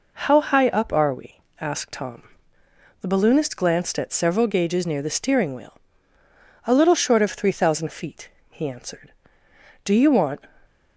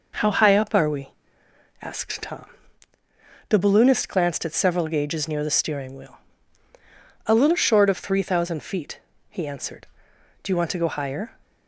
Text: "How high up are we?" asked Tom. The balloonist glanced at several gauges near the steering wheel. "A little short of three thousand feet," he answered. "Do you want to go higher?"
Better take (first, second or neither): second